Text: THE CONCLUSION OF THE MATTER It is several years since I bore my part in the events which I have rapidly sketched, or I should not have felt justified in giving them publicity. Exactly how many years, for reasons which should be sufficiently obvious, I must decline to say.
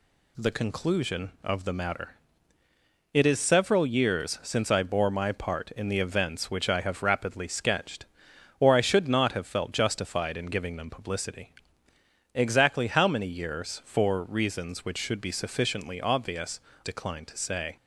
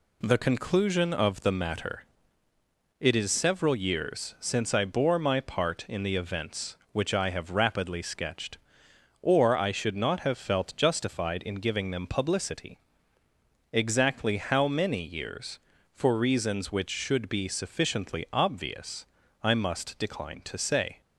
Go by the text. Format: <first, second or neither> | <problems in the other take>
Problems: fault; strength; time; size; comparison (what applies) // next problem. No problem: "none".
second | pauses between "MATTER" and "It"; noticeable; at 2.1 s; 0.98 s long; noticeable in the second // skips "I must"; at 16.7 s